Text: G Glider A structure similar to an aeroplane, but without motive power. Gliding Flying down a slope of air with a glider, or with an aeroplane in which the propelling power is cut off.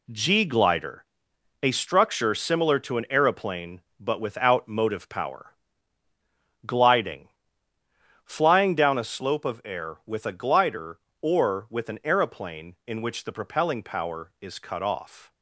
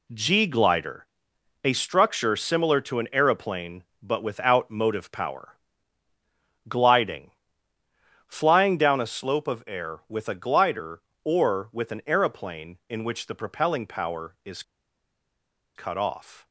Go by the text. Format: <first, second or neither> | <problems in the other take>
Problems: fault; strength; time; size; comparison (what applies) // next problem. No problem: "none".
first | pauses between "Glider" and "A"; noticeable; at 1.0 s; 0.56 s long; noticeable in the first // pauses between "Gliding" and "Flying"; noticeable; at 7.3 s; 0.96 s long; noticeable in the first // pauses between "is" and "cut"; at 14.6 s; 1.1 s long